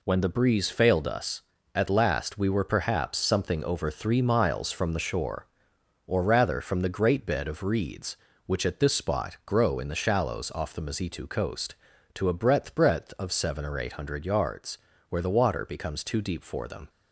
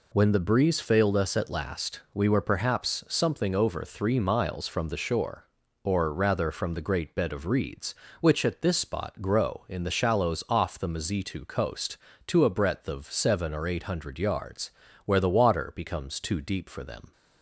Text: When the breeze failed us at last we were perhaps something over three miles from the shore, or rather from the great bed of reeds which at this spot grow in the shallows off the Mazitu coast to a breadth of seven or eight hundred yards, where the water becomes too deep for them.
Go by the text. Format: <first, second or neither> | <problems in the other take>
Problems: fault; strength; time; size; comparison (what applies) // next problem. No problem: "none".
second | says "breadth" twice; at 12.7 s